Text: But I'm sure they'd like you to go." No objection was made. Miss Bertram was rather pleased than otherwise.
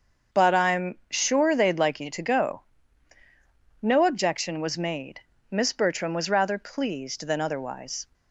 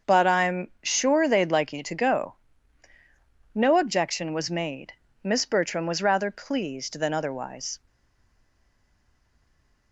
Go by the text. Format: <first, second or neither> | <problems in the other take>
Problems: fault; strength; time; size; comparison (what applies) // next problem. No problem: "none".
first | starts louder than the rest; until 1.1 s; 6.5 dB; also in the first // stays silent after the last word; from 7.8 s on; 2.1 s long